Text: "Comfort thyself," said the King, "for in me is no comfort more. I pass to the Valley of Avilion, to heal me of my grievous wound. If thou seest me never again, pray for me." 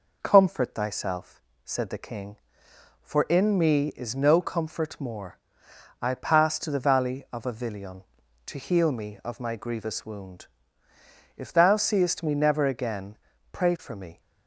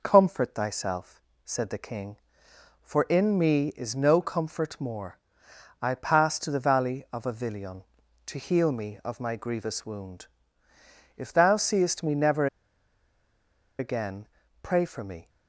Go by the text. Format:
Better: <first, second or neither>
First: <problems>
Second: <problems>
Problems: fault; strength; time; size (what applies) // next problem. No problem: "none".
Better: first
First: none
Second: pauses between "never" and "again"; strong; at 12.4 s; 1.3 s long